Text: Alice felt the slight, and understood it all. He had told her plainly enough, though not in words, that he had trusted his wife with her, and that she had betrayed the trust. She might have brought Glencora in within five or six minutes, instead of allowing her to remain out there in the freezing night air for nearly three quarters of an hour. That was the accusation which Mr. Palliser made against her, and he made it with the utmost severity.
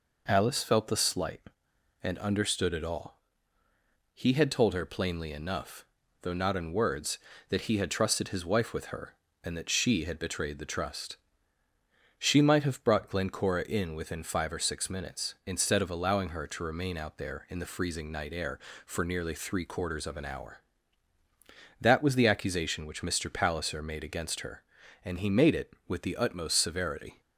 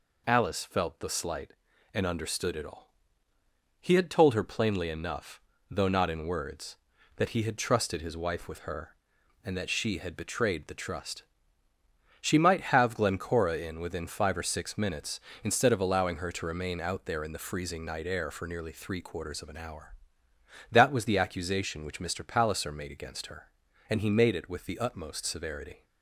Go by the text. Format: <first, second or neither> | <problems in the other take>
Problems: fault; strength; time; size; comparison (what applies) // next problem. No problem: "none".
first | skips "brought"; at 12.9 s